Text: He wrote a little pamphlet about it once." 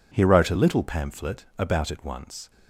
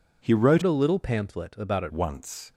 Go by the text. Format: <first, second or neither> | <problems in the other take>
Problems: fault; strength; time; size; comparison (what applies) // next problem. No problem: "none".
first | changes voice from "a" to "it"; from 0.6 to 1.9 s; 1.3 s long